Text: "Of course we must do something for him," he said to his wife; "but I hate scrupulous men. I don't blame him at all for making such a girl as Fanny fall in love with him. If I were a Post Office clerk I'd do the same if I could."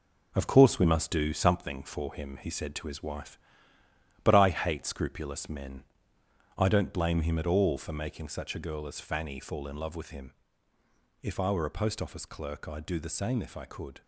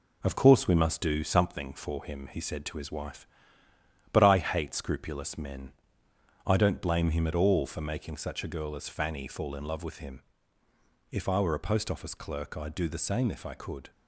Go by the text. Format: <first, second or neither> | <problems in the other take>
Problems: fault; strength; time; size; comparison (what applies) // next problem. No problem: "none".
second | gets quieter; throughout; 6.5 dB